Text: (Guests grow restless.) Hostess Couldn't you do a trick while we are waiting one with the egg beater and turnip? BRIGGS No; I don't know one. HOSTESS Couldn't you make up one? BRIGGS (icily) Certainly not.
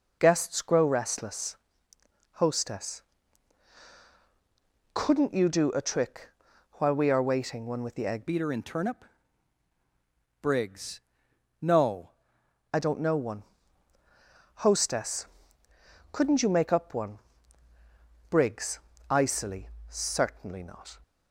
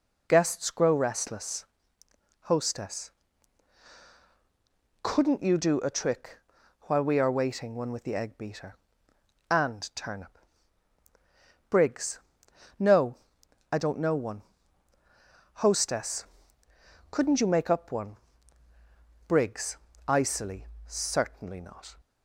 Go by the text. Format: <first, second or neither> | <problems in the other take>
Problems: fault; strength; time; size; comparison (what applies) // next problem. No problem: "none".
second | pauses between "Hostess" and "Couldn't"; strong; at 3.0 s; 1.9 s long; strong in the second // pauses between "trick" and "while"; noticeable; at 6.2 s; 0.46 s long; noticeable in the second // changes voice from "beater" to "No"; from 8.2 to 12.1 s; 3.9 s long // pauses between "BRIGGS" and "No"; noticeable; at 11.0 s; 0.62 s long; noticeable in the second // pauses between "HOSTESS" and "Couldn't"; noticeable; at 15.2 s; 0.84 s long; noticeable in the second